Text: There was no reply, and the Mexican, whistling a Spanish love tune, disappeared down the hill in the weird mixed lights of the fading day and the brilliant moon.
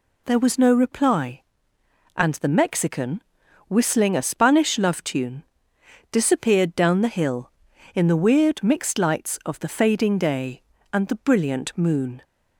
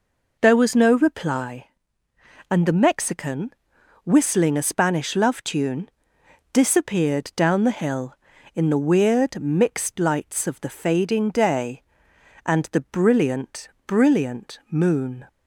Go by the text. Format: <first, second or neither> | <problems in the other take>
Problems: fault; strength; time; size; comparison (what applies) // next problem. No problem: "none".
first | says "brilliant" twice; at 13.8 s